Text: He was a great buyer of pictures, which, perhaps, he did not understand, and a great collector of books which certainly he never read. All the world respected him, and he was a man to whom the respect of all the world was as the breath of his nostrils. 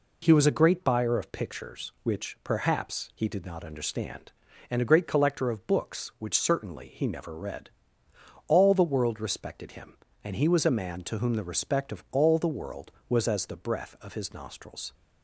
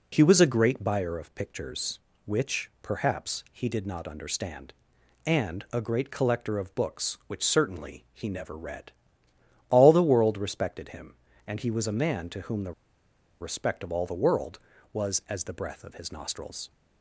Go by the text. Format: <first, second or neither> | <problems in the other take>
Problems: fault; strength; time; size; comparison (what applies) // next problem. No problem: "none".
first | pauses between "the" and "respect"; noticeable; at 12.7 s; 0.69 s long